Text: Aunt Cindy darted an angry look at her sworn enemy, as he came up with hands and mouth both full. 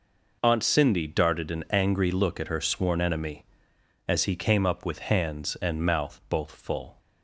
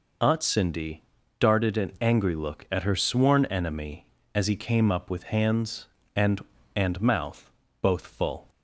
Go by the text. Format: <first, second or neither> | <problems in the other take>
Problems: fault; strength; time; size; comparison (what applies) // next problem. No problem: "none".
first | pauses between "Cindy" and "darted"; slight; at 1.0 s; 0.36 s long // says "and" twice; at 6.7 s // pauses between "mouth" and "both"; slight; at 7.5 s; 0.30 s long